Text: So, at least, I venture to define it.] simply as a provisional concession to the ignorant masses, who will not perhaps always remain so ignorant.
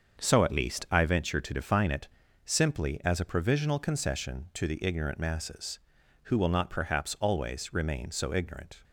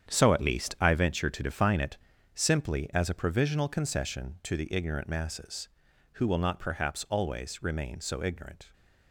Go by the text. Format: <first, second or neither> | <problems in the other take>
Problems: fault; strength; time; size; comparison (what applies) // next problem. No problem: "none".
first | gets quieter; strong; throughout; 11 dB // starts louder than the rest; strong; until 1.1 s; 8.5 dB; also in the first